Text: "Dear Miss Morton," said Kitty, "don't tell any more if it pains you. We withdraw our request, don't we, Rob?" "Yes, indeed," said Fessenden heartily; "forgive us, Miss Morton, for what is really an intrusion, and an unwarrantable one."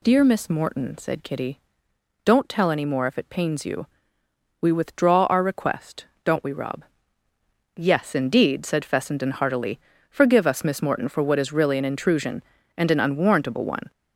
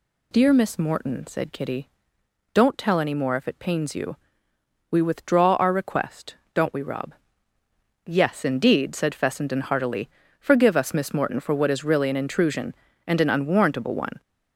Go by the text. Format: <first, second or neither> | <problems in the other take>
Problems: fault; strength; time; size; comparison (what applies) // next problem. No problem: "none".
neither | none